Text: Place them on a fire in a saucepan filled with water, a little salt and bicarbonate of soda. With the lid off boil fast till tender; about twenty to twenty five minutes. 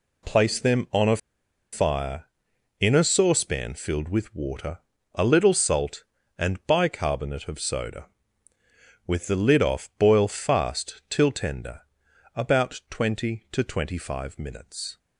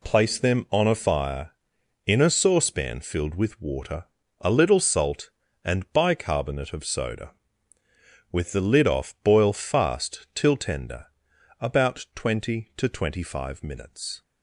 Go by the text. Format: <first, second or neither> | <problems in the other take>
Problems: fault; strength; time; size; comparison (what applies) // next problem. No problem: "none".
second | pauses between "a" and "fire"; noticeable; at 1.1 s; 0.55 s long